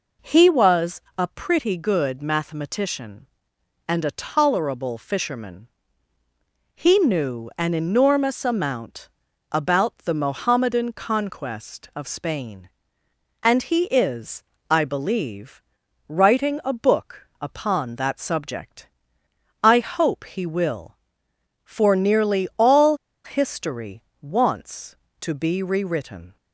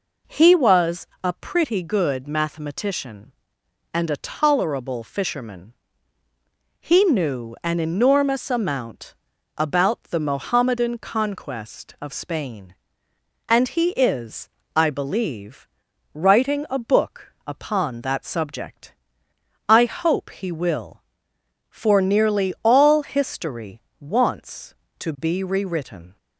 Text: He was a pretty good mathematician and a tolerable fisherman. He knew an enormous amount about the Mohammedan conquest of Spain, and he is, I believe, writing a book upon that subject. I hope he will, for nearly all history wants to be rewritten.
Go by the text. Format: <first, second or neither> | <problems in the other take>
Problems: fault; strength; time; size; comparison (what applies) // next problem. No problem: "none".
second | pauses between "was" and "a"; slight; at 1.0 s; 0.16 s long; slight in the second // pauses between "amount" and "about"; at 9.0 s; 0.42 s long; also in the second // pauses between "all" and "history"; slight; at 22.9 s; 0.27 s long // pauses between "history" and "wants"; slight; at 24.0 s; 0.22 s long; slight in the second